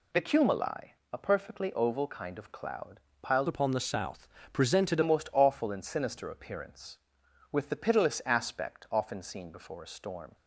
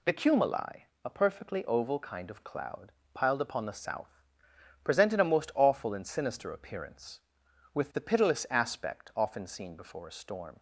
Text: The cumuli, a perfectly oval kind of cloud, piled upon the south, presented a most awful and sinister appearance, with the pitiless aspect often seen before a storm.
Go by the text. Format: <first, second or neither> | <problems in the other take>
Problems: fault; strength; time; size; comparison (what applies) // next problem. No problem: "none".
second | changes voice from "upon" to "presented"; from 3.4 to 5.0 s; 1.6 s long